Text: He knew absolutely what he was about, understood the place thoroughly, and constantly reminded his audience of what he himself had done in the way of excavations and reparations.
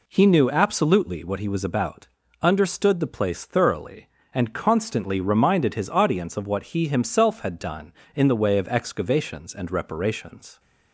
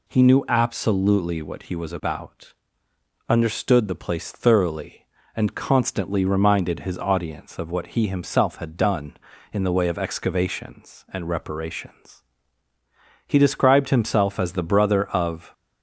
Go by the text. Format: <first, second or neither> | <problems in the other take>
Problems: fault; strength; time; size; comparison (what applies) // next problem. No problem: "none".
first | goes on to say "He described himself as the brother of"; strong; from 13.2 s on; 2.2 s long